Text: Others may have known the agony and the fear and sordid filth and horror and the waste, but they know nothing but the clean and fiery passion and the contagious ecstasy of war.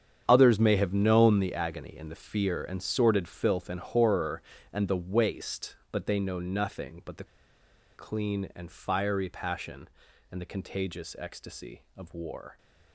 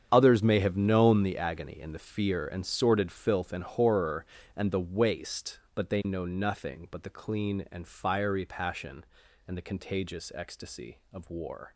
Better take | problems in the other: second | starts louder than the rest; strong; until 1.2 s; 8.5 dB; strong in the second // pauses between "the" and "clean"; noticeable; at 7.2 s; 0.71 s long

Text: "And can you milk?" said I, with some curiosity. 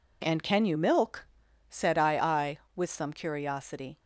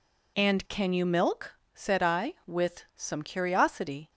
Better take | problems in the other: second | says "I" twice; at 2.1 s

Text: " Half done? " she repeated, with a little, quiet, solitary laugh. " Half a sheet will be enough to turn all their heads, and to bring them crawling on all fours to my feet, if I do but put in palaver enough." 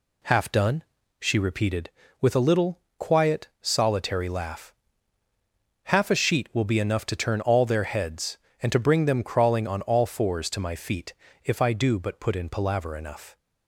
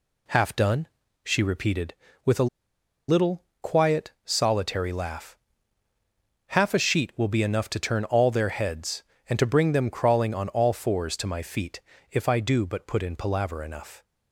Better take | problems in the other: first | pauses between "a" and "little"; noticeable; at 2.4 s; 0.61 s long

